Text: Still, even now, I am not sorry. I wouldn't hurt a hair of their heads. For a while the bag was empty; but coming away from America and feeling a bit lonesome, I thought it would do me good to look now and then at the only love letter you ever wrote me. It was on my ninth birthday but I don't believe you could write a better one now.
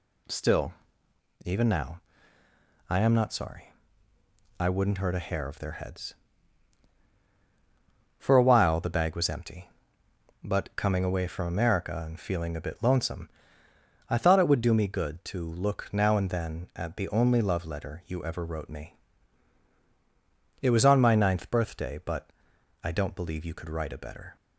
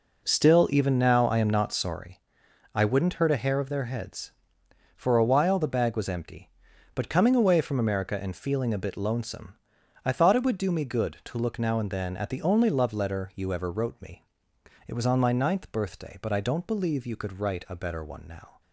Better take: second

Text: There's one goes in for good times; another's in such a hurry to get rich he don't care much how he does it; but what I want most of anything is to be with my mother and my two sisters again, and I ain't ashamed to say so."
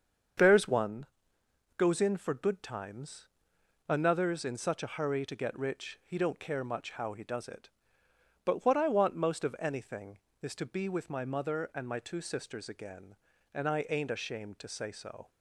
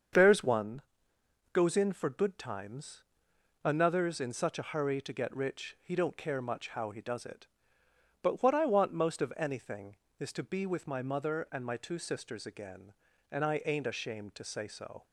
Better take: neither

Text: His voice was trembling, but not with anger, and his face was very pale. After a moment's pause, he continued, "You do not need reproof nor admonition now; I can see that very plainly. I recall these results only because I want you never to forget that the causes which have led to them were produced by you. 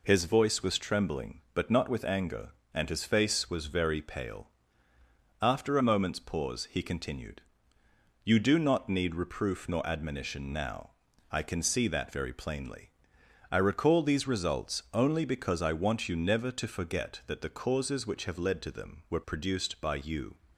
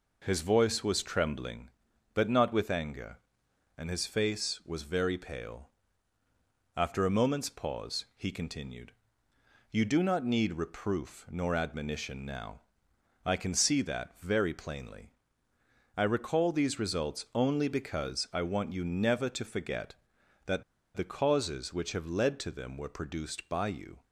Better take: first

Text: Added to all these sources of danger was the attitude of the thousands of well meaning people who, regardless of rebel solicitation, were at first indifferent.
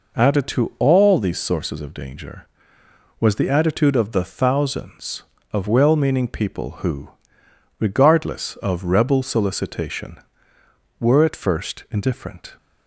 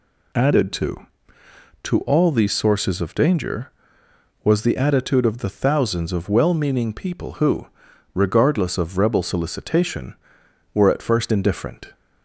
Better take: first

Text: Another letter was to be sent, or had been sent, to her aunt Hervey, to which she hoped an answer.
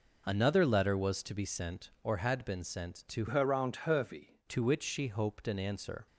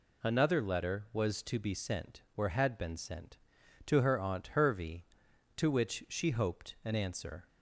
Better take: second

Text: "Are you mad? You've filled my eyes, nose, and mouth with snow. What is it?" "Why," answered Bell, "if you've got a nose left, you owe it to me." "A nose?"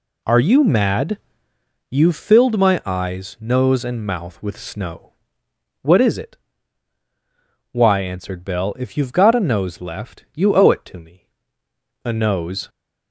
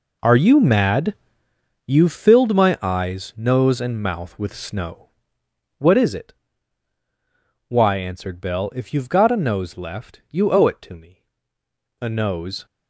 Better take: first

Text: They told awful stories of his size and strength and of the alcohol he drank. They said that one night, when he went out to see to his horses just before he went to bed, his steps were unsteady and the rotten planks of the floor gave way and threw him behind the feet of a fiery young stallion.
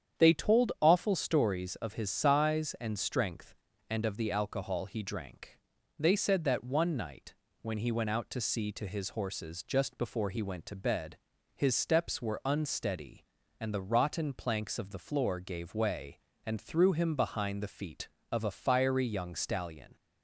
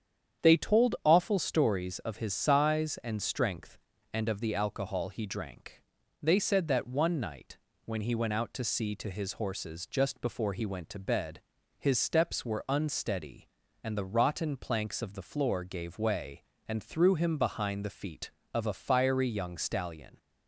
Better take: neither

